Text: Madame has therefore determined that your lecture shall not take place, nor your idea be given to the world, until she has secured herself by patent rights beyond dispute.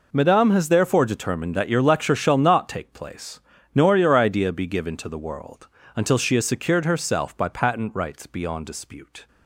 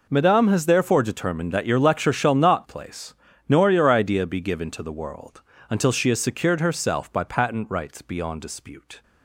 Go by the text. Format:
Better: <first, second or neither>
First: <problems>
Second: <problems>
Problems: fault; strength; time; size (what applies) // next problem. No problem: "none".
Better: first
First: none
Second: skips "take"; at 2.6 s